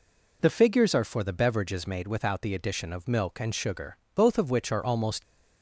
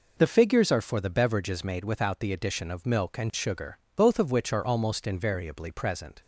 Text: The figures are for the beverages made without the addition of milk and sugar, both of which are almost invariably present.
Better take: second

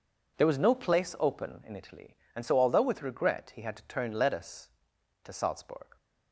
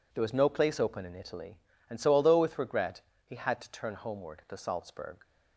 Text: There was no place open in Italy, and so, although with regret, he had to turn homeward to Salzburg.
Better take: second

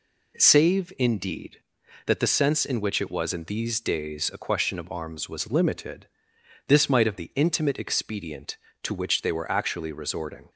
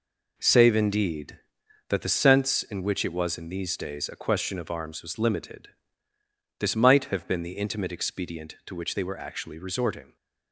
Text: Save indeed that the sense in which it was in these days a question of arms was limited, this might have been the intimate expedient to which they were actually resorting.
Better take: second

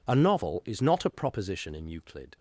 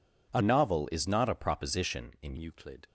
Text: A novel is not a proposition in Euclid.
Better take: first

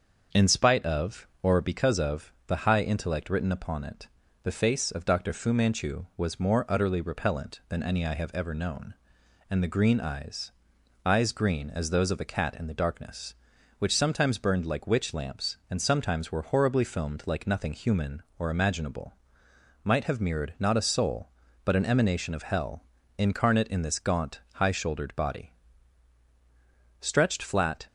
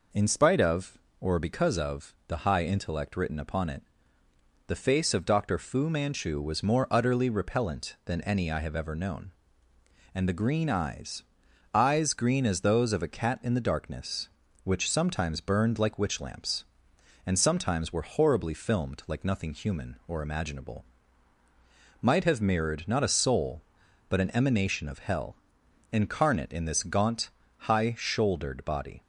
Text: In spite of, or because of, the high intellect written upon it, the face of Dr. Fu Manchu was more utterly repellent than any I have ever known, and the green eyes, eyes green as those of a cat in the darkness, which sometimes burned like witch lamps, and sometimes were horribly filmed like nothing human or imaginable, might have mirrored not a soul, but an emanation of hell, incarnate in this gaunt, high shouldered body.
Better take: second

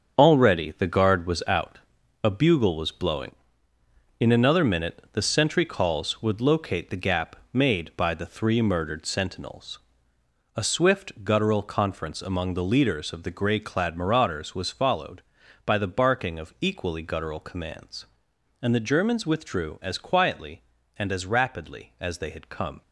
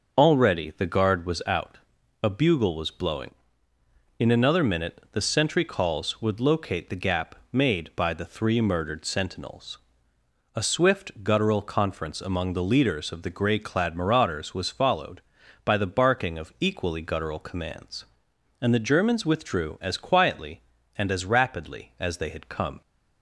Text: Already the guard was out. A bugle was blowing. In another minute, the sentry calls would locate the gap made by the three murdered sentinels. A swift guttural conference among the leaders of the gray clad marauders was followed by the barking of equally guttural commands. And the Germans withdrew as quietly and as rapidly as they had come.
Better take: second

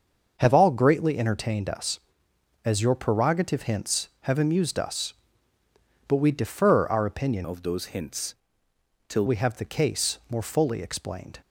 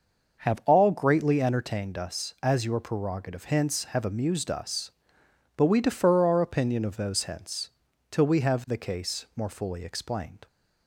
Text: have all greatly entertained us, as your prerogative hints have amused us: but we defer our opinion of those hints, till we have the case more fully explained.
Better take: second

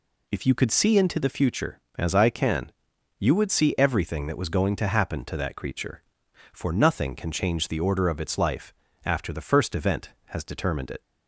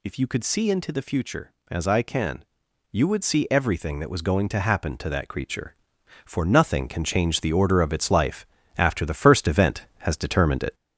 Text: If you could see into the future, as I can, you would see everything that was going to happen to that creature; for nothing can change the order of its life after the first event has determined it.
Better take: first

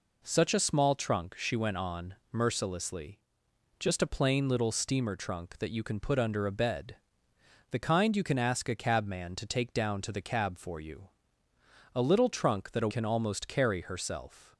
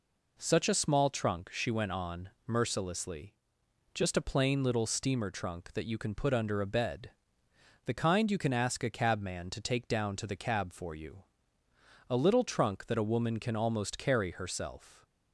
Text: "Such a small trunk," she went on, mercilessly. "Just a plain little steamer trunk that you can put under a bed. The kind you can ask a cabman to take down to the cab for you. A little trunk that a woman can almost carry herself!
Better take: second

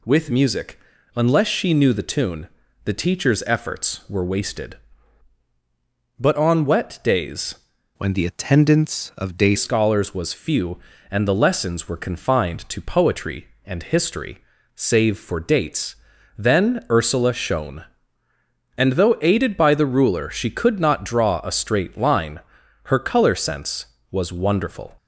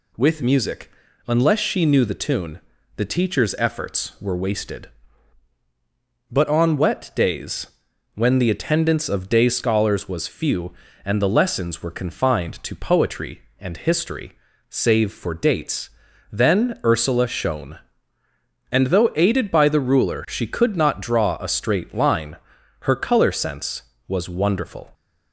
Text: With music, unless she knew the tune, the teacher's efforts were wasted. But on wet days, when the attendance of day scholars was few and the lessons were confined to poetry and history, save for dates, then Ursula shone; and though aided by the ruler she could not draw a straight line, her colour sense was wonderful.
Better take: second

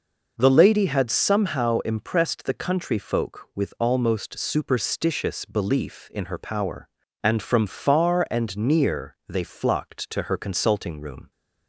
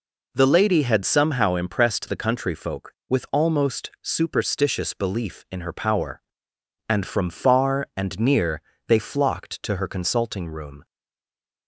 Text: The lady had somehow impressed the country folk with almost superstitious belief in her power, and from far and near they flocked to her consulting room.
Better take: first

